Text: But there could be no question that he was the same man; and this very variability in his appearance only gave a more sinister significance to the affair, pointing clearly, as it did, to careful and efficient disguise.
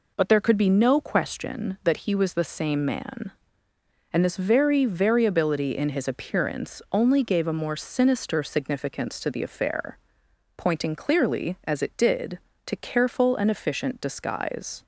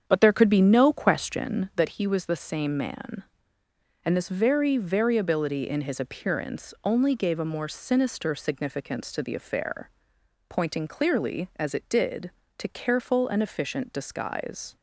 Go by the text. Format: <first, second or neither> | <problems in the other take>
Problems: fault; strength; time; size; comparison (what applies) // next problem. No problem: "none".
first | starts louder than the rest; strong; until 1.9 s; 8 dB